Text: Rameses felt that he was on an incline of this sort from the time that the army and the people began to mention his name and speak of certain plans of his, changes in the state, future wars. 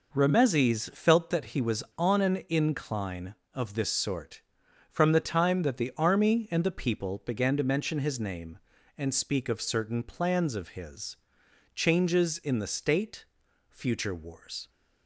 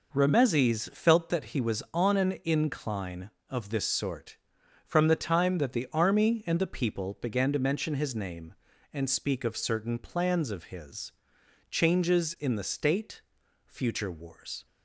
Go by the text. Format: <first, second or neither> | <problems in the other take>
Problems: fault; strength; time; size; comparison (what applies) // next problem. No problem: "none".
neither | none